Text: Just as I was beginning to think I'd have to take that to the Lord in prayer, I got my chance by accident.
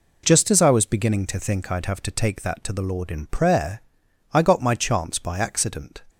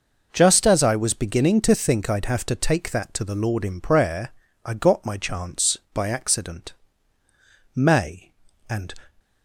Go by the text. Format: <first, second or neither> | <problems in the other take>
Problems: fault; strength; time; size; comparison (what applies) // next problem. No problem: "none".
first | goes on to say "May and"; noticeable; from 7.7 s on; 1.2 s long